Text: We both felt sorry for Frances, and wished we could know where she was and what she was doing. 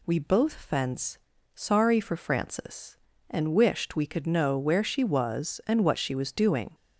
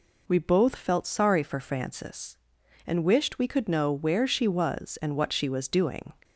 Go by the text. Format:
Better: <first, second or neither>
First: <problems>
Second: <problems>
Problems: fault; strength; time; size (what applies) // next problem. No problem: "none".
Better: second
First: says "fence" for "felt"; at 0.5 s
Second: none